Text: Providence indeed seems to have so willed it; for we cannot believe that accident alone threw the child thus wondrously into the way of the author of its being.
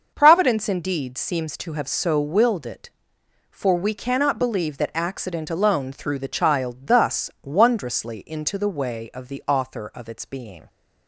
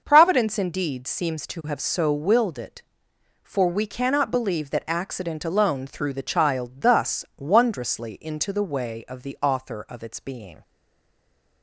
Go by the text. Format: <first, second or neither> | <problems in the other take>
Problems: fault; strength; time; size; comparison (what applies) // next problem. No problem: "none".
first | starts louder than the rest; until 1.0 s; 6 dB; also in the first // stays silent after the last word; from 10.6 s on; 1.0 s long